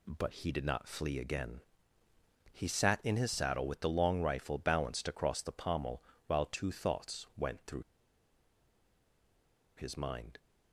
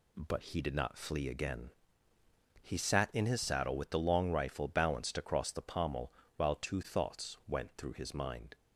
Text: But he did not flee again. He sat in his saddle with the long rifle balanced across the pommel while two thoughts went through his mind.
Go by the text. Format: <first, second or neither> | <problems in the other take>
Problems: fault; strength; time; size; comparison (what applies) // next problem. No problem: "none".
second | pauses between "pommel" and "while"; slight; at 6.0 s; 0.24 s long; slight in the second // pauses between "through" and "his"; strong; at 7.8 s; 1.9 s long